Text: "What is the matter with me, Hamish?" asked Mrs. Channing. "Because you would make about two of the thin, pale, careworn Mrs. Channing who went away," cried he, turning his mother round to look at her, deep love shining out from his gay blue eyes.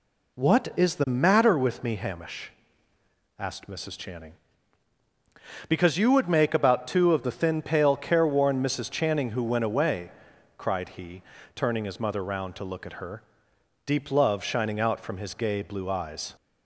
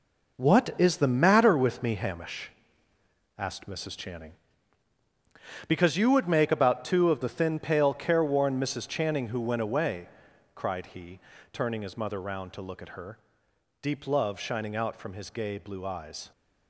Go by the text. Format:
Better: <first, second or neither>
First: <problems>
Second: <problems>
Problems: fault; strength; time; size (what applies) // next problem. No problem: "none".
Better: first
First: none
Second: gets quieter; strong; throughout; 9 dB